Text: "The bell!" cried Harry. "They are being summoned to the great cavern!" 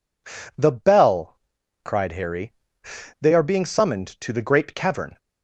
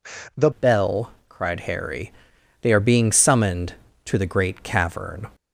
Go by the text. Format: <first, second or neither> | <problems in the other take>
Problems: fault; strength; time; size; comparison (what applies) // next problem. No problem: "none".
first | changes voice at "bell"; from 0.5 s on; 4.7 s long